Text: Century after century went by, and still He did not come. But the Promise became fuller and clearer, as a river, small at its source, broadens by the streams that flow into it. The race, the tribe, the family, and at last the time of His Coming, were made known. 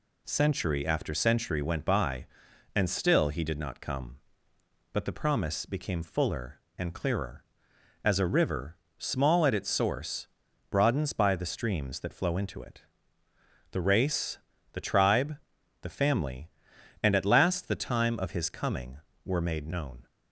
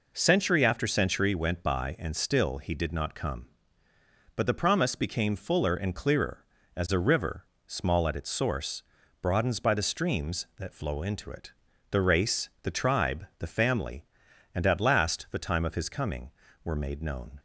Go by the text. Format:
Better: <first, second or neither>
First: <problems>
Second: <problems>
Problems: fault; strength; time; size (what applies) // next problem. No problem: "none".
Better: neither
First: none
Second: none